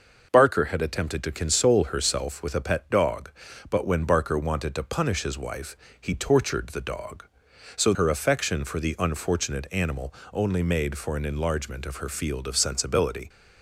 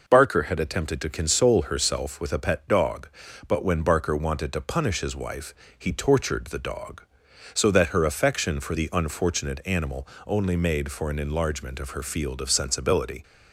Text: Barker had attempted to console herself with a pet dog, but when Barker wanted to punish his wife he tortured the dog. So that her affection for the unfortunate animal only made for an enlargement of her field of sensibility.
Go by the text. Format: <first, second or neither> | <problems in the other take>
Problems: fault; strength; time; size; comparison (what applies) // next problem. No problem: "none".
second | pauses between "wife" and "he"; slight; at 5.7 s; 0.24 s long; slight in the second // skips "that"; at 7.9 s // pauses between "animal" and "only"; slight; at 10.1 s; 0.20 s long; slight in the second